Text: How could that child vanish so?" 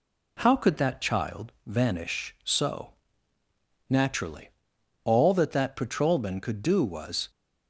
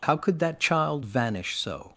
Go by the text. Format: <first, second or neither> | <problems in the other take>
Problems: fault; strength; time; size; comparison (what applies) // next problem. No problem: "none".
second | goes on to say "Naturally all that that patrolman could do was"; strong; from 3.8 s on; 3.4 s long